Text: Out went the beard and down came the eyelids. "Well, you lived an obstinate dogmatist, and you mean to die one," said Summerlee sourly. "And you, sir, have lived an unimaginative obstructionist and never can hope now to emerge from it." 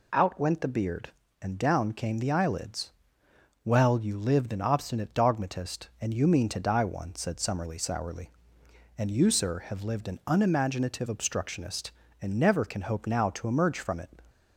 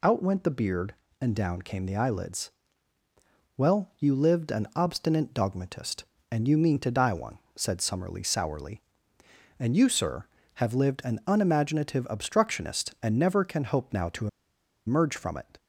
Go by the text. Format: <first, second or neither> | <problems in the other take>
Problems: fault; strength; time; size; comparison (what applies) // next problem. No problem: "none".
first | pauses between "to" and "emerge"; noticeable; at 14.2 s; 0.59 s long